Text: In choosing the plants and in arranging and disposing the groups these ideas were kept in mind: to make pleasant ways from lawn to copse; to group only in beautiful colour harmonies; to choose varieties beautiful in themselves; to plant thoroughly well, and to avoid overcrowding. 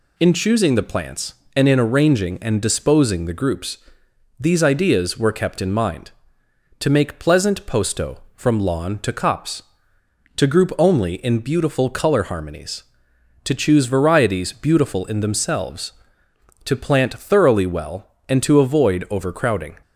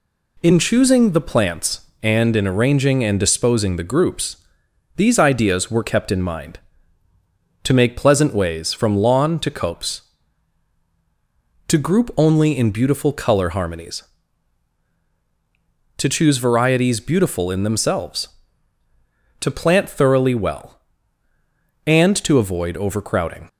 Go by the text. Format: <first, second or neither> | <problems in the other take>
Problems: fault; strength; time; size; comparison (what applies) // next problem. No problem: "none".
second | pauses between "groups" and "these"; noticeable; at 3.7 s; 0.62 s long; noticeable in the second // says "posto" for "ways"; at 7.6 s